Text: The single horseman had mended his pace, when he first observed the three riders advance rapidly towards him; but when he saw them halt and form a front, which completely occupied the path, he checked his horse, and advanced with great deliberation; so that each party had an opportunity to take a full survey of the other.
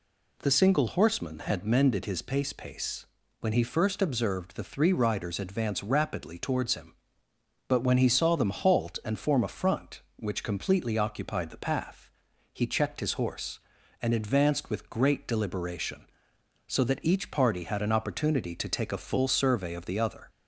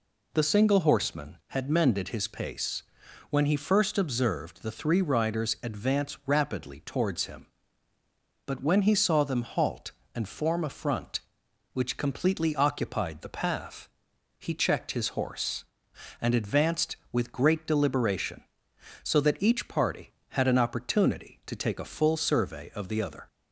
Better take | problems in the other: second | says "pace" twice; at 2.5 s

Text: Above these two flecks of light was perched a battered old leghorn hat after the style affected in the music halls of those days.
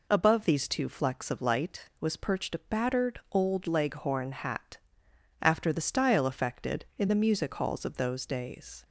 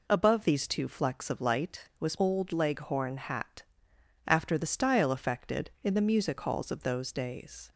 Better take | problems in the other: first | skips "perched a battered"; at 2.1 s // pauses between "hat" and "after"; noticeable; at 3.6 s; 0.64 s long; noticeable in the first

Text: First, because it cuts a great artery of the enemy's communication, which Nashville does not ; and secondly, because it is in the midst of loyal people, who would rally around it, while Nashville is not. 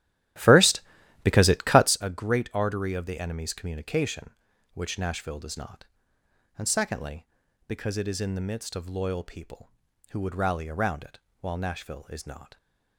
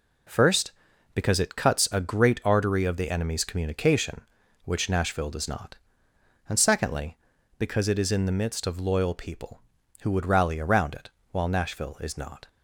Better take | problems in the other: second | starts louder than the rest; strong; until 2.0 s; 13.5 dB

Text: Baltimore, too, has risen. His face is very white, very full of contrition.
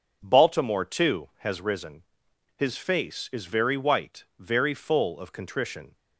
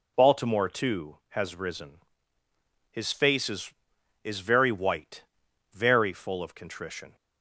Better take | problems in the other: first | says "is" twice; at 4.2 s

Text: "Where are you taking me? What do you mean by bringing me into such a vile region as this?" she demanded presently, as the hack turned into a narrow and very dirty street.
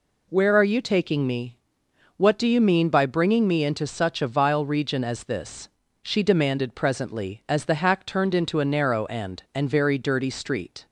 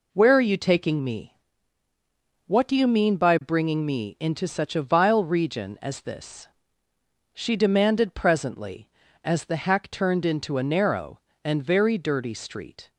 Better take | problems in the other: second | says "and" twice; at 9.5 s

